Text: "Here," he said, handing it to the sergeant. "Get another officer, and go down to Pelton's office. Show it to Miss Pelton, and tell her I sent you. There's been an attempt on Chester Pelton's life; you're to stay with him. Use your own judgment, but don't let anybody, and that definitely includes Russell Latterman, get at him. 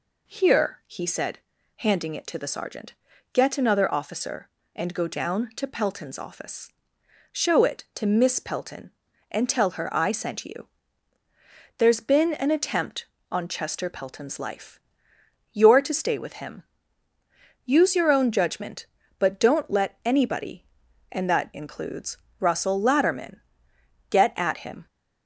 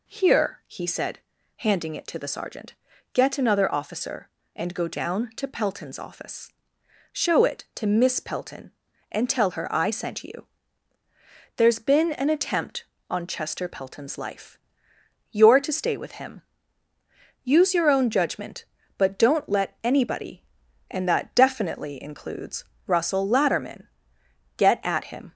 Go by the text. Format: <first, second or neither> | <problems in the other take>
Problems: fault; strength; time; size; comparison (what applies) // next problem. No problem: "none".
second | skips "definitely"; at 21.5 s // pauses between "includes" and "Russell"; slight; at 22.1 s; 0.22 s long; slight in the second